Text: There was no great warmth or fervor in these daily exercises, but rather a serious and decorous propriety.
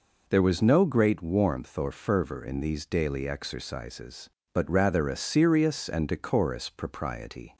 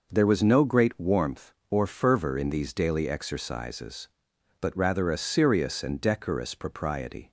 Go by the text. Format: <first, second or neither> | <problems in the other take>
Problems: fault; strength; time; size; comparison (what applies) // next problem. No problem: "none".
neither | none